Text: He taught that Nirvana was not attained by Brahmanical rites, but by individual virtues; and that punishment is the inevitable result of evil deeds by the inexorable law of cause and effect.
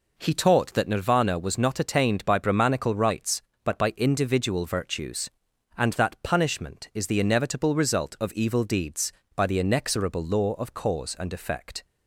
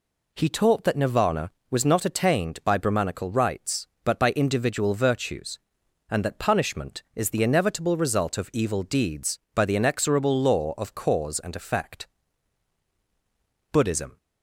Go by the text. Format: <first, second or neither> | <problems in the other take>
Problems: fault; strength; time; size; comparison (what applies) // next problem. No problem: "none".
first | goes on to say "Buddhism"; slight; from 13.7 s on; 0.44 s long